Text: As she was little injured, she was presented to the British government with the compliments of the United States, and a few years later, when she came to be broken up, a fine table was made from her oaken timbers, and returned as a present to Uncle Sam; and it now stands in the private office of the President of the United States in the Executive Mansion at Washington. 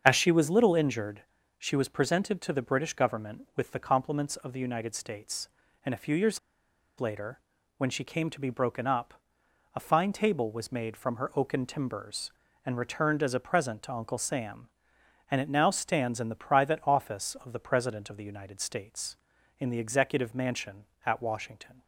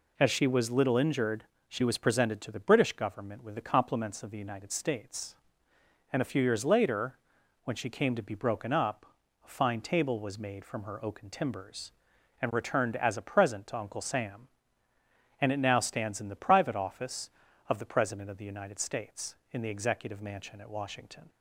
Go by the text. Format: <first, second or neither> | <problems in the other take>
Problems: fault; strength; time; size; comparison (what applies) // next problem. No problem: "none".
second | starts louder than the rest; until 1.0 s; 7 dB // pauses between "years" and "later"; noticeable; at 6.3 s; 0.60 s long